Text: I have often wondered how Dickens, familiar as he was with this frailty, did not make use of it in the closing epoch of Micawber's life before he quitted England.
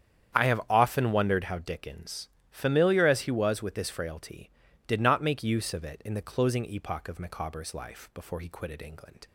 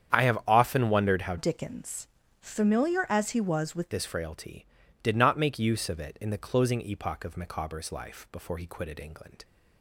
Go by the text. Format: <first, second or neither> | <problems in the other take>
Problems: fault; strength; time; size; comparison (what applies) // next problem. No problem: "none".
first | starts louder than the rest; strong; until 1.1 s; 8.5 dB; strong in the first // changes voice from "Dickens" to "with"; from 1.3 to 3.9 s; 2.6 s long